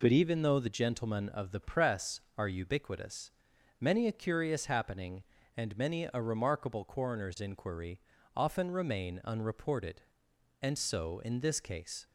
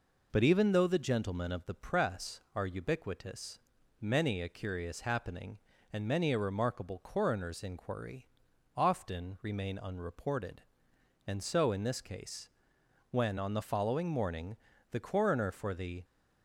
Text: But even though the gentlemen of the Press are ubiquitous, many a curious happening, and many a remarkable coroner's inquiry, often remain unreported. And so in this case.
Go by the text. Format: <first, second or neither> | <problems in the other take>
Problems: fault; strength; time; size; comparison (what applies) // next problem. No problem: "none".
first | goes on to say "When on the following morning the coroner for the"; strong; from 13.1 s on; 2.9 s long